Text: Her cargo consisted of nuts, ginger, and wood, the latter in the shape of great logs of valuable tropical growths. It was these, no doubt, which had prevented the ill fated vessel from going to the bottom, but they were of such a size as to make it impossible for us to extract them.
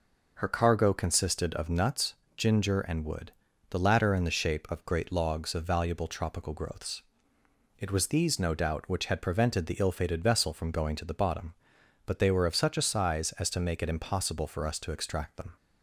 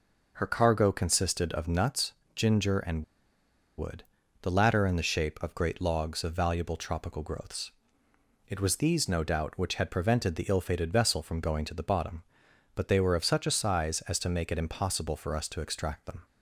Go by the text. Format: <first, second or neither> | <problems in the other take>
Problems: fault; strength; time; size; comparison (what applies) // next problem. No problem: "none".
first | pauses between "and" and "wood"; noticeable; at 3.0 s; 0.76 s long